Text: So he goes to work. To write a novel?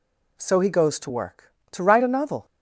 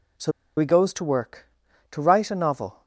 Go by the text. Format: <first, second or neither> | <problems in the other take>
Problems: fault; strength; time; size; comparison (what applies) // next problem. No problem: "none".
first | pauses between "So" and "he"; slight; at 0.3 s; 0.26 s long